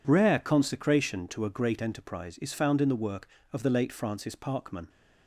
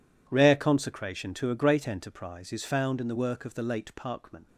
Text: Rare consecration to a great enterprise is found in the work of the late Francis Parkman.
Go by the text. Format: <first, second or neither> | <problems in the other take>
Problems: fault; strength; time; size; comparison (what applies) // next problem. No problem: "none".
first | skips "Francis"; at 3.9 s